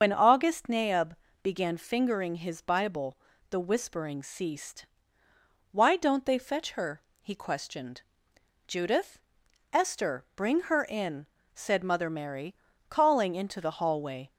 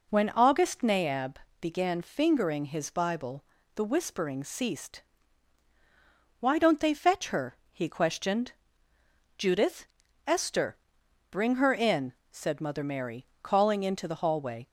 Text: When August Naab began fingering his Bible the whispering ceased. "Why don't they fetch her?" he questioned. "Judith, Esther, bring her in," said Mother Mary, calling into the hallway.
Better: second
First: loses the start of "When"; at 0.0 s; 95 ms // starts louder than the rest; until 1.0 s; 6.5 dB // pauses between "Naab" and "began"; slight; at 1.1 s; 0.26 s long // pauses between "Bible" and "the"; slight; at 3.1 s; 0.32 s long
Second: pauses between "Naab" and "began"; slight; at 1.3 s; 0.26 s long // pauses between "Bible" and "the"; slight; at 3.4 s; 0.32 s long

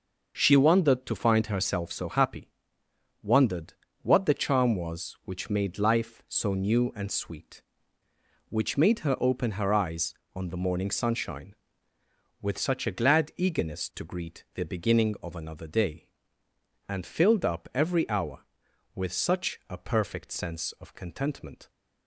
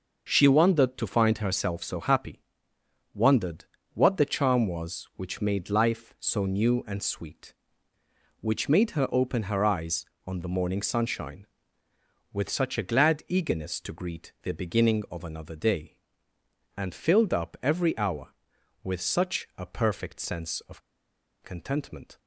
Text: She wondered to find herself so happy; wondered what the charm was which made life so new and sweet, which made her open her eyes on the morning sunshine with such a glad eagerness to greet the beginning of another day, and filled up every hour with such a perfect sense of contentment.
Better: first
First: starts louder than the rest; noticeable; until 1.3 s; 6 dB // pauses between "wondered" and "what"; slight; at 3.7 s; 0.30 s long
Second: starts louder than the rest; noticeable; until 1.3 s; 6 dB // pauses between "wondered" and "what"; slight; at 3.6 s; 0.30 s long // pauses between "of" and "contentment"; noticeable; at 20.8 s; 0.63 s long

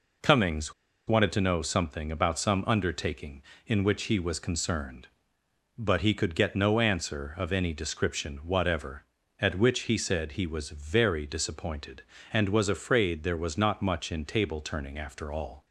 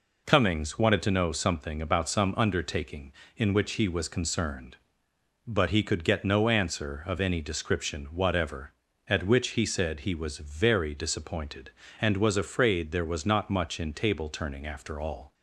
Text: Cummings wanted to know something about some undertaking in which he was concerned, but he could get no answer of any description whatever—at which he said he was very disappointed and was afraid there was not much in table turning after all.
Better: second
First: pauses between "Cummings" and "wanted"; slight; at 0.7 s; 0.33 s long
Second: none

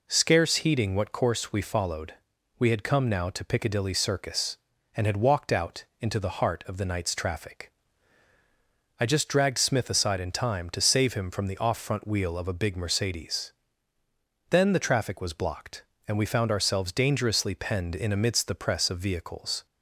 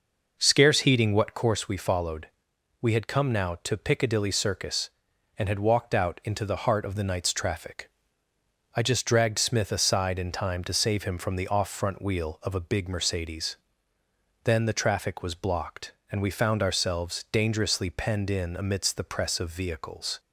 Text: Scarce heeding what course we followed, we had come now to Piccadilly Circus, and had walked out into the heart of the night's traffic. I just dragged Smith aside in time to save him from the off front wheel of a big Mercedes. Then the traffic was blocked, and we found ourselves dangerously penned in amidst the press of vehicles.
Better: first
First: none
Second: starts louder than the rest; noticeable; until 1.6 s; 5.5 dB

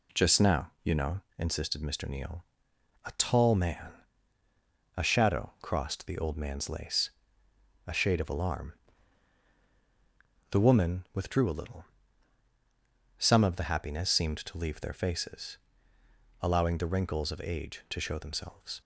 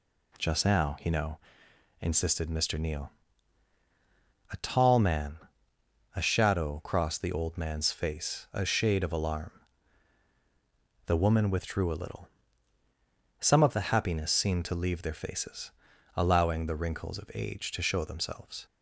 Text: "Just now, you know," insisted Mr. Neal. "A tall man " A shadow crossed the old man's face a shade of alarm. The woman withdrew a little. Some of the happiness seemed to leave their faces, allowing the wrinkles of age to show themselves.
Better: second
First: says "lace" for "face"; at 6.6 s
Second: none

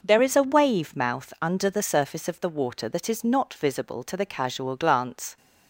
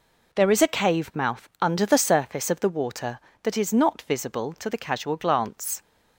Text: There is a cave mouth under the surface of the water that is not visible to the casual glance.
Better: second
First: says "wave" for "cave"; at 0.4 s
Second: none

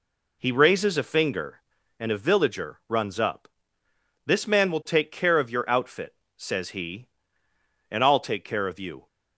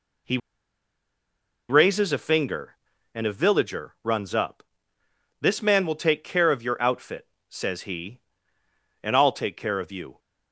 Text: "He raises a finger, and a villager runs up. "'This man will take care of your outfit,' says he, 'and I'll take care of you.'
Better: first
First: none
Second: pauses between "He" and "raises"; strong; at 0.3 s; 1.3 s long

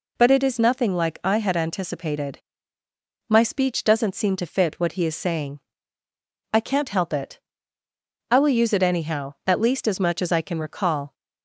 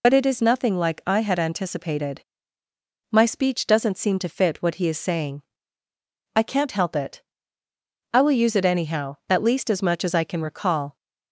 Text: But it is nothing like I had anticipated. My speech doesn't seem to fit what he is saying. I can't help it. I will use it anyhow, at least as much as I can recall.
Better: first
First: none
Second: loses the start of "But"; at 0.0 s; 50 ms

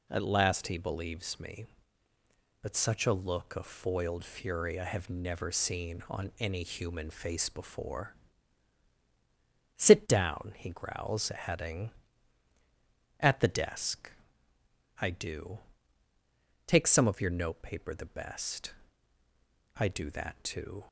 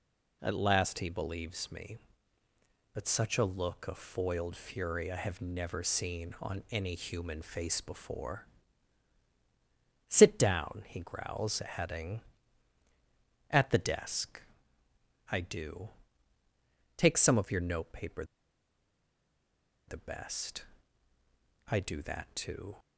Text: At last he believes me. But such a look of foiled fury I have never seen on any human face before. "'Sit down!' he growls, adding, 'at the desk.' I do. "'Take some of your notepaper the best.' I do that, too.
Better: first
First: none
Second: pauses between "notepaper" and "the"; strong; at 18.2 s; 1.6 s long

